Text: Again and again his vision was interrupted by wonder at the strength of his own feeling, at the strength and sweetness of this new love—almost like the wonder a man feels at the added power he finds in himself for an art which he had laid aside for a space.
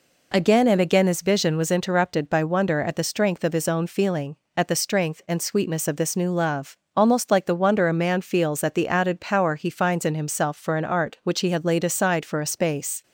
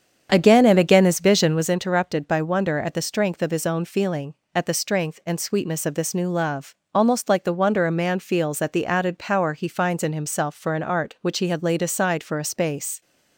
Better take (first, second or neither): first